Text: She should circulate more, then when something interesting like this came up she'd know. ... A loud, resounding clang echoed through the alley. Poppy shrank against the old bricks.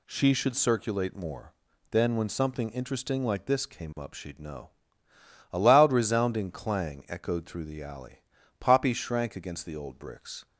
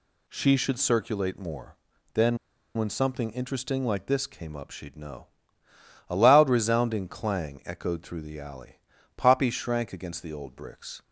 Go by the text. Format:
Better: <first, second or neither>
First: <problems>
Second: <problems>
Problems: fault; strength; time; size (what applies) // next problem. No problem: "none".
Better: first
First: none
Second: pauses between "then" and "when"; at 2.3 s; 0.39 s long